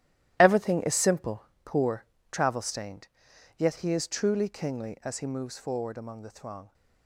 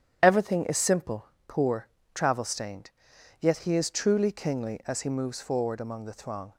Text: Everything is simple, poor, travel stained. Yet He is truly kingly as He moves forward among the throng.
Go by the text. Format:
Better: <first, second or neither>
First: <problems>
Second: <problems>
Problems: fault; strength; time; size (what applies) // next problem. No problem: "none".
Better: second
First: gets quieter; strong; throughout; 12 dB // starts louder than the rest; strong; until 1.4 s; 13.5 dB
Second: starts louder than the rest; strong; until 1.2 s; 9.5 dB